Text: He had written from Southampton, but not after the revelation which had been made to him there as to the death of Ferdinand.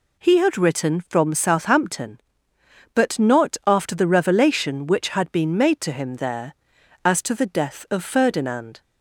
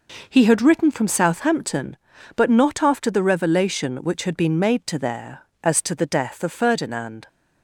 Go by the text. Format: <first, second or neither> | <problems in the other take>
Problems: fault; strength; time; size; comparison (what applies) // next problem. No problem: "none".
first | skips "him"; at 4.9 s